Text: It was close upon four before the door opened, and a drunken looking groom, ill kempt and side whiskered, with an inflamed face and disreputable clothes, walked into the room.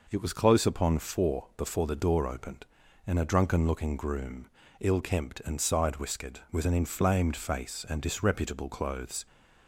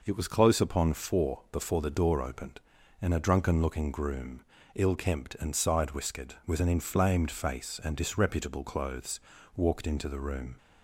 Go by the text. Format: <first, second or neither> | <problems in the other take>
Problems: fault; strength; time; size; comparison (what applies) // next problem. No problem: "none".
second | stops before "walked into the room"; at 9.2 s